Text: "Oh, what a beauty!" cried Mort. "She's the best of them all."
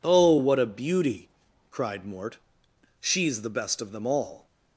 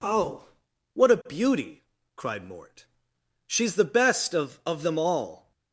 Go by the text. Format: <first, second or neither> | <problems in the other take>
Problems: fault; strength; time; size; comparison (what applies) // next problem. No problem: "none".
first | says "of" twice; at 4.6 s